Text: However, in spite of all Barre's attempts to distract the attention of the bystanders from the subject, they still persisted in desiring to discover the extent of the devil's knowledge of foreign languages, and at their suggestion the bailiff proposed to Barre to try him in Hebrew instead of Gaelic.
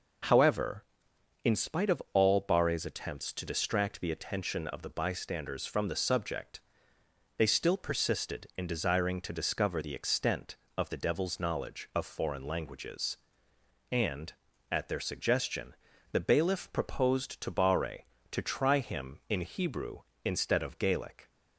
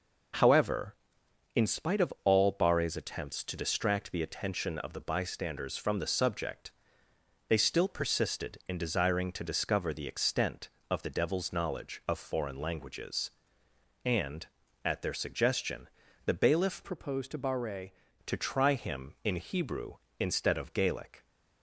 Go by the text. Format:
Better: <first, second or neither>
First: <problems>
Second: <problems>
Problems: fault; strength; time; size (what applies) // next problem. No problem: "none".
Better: first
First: pauses between "suggestion" and "the"; slight; at 15.7 s; 0.36 s long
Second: pauses between "suggestion" and "the"; slight; at 15.8 s; 0.36 s long // changes voice from "proposed" to "Barre"; from 16.8 to 17.9 s; 1.1 s long